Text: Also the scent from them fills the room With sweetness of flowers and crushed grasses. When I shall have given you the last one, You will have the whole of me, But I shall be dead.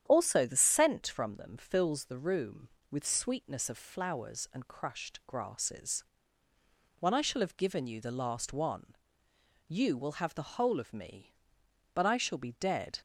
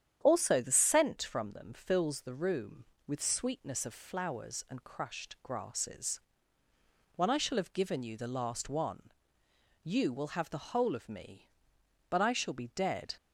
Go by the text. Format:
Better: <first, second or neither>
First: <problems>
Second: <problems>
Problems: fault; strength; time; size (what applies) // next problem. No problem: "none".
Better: neither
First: starts louder than the rest; strong; until 1.0 s; 9.5 dB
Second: starts louder than the rest; strong; until 1.2 s; 9.5 dB